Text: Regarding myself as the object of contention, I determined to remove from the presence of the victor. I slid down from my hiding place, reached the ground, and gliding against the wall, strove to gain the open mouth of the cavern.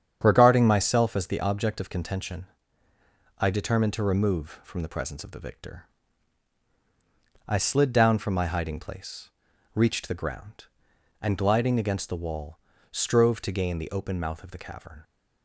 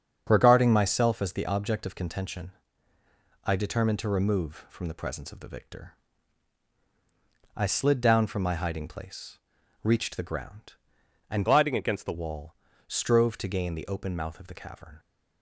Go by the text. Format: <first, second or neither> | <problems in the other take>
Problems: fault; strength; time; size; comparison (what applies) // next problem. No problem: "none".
first | starts louder than the rest; until 1.2 s; 7 dB; strong in the first // changes voice from "gliding" to "the"; from 11.4 to 12.1 s; 0.7 s long